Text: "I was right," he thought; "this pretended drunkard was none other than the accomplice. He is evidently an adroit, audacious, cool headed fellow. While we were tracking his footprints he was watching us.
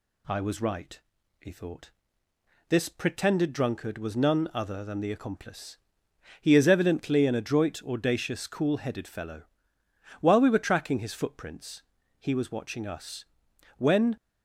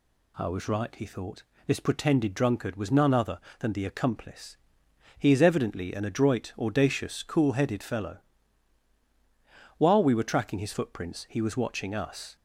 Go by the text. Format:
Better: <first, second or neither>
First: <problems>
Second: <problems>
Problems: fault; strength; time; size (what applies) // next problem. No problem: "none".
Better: second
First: pauses between "footprints" and "he"; at 11.8 s; 0.38 s long // goes on to say "When"; slight; from 13.7 s on; 0.40 s long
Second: none